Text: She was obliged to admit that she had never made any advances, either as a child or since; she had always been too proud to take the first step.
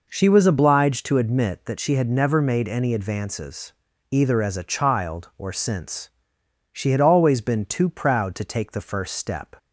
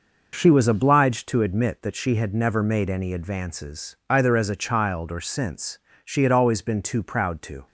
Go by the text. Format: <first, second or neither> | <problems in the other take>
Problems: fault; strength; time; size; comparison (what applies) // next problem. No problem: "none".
first | stops before "take the first step"; at 7.6 s